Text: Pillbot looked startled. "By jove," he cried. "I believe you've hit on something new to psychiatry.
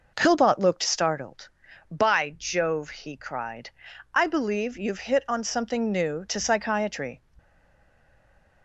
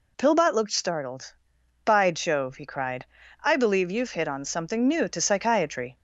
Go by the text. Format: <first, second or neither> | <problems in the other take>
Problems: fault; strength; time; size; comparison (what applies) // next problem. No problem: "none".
second | stays silent after the last word; noticeable; from 7.3 s on; 1.3 s long